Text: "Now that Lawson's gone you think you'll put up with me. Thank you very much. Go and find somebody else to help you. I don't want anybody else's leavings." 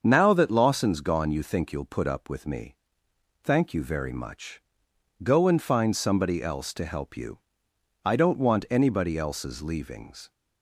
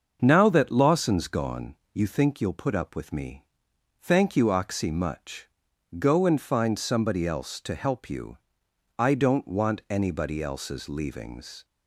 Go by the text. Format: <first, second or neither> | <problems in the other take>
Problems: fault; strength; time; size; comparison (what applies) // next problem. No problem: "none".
first | starts louder than the rest; until 1.2 s; 6.5 dB; also in the first // pauses between "gone" and "you"; slight; at 1.7 s; 0.18 s long // says "oxy" for "very"; at 4.5 s